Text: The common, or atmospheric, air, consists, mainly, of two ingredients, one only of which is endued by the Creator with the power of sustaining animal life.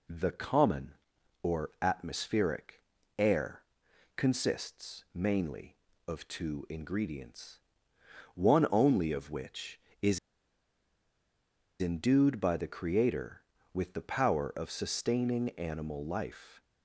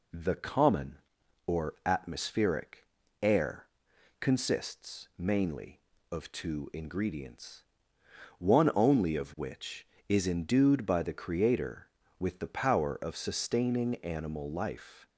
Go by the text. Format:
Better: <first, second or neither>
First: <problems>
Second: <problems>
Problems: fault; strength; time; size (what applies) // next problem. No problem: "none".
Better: second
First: pauses between "is" and "endued"; strong; at 10.1 s; 1.6 s long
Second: none